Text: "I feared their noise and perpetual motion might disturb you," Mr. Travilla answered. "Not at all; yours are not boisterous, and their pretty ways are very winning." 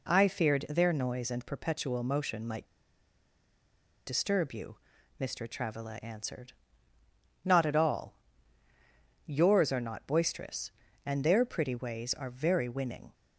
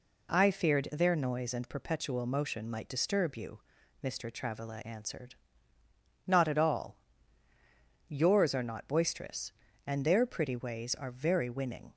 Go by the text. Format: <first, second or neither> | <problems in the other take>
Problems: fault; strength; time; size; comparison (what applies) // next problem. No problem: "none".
second | pauses between "might" and "disturb"; strong; at 2.6 s; 1.4 s long